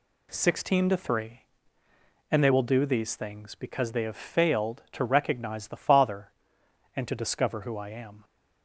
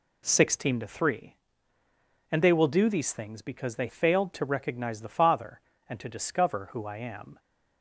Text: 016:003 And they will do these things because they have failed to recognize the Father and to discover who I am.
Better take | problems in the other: first | skips "have"; at 3.8 s

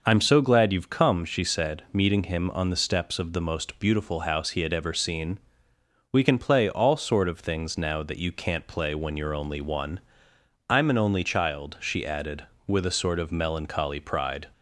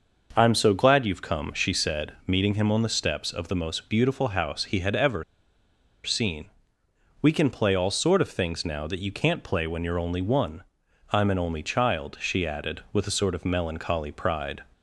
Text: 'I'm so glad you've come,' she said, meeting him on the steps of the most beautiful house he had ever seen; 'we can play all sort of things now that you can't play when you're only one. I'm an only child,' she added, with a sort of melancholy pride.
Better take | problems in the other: first | starts louder than the rest; noticeable; until 1.3 s; 6 dB // pauses between "ever" and "seen"; noticeable; at 5.2 s; 0.81 s long

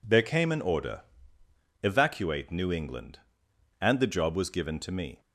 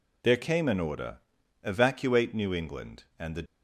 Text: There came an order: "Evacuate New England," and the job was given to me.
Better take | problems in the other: first | stops before "job was given to me"; at 3.4 s

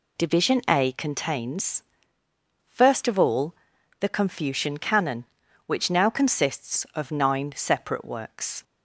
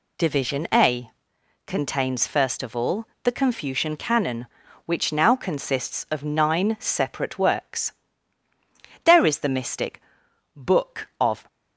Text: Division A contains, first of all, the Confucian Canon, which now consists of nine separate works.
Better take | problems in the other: first | pauses between "A" and "contains"; noticeable; at 1.0 s; 0.56 s long // goes on to say "There is the mystic Book of"; strong; from 9.0 s on; 2.4 s long

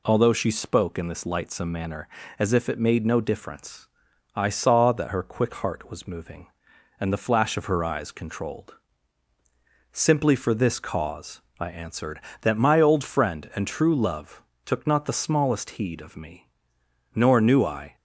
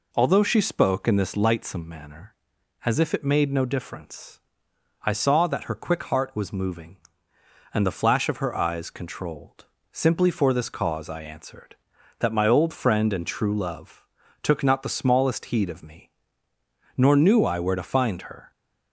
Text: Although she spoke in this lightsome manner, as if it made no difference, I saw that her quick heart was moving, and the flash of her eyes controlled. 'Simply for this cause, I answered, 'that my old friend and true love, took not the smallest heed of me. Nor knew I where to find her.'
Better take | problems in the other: second | stops before "where to find her"; at 17.9 s

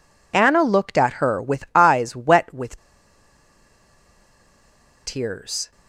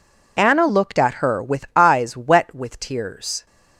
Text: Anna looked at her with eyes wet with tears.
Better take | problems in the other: second | pauses between "with" and "tears"; strong; at 2.7 s; 2.2 s long

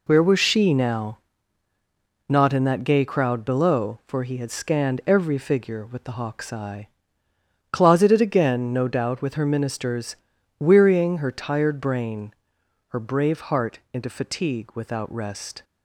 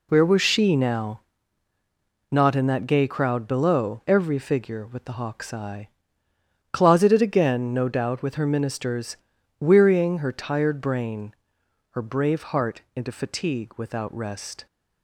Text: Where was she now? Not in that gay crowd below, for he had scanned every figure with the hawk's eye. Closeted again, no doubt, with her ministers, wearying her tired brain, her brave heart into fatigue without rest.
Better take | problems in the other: first | skips "for he had scanned"; at 4.0 s

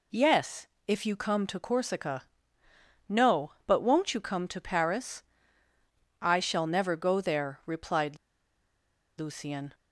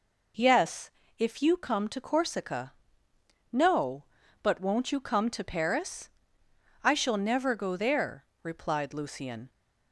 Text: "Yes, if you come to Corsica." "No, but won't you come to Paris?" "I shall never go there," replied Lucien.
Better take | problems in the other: second | pauses between "replied" and "Lucien"; at 8.1 s; 1.0 s long

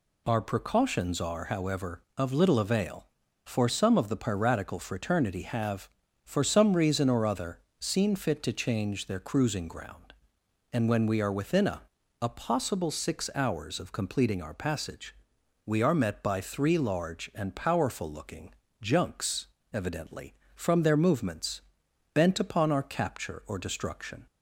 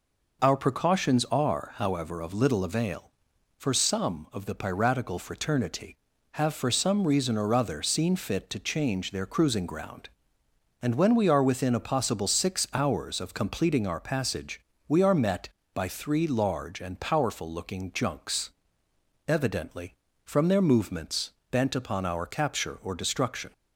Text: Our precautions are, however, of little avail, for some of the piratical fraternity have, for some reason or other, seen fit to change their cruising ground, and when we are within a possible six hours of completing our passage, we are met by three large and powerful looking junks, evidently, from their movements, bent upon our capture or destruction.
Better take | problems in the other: second | says "a" twice; at 12.2 s // pauses between "looking" and "junks"; slight; at 18.5 s; 0.30 s long

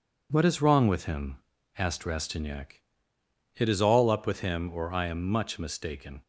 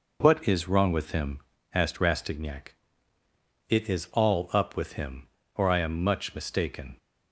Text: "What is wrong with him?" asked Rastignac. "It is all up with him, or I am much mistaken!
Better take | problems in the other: neither | none

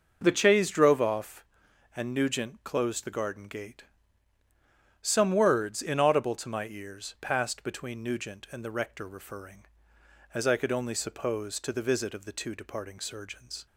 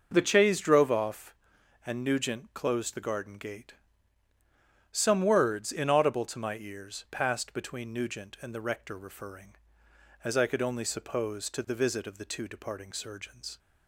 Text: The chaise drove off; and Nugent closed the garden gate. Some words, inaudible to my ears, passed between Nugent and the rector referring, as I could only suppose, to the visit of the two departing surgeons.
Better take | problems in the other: neither | starts louder than the rest; noticeable; the same in both

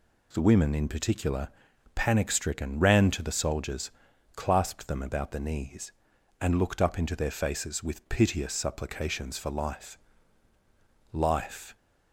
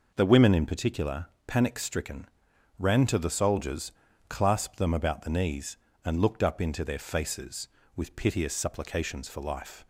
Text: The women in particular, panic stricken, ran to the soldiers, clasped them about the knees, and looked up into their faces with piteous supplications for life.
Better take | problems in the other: second | says "life" twice; at 11.1 s

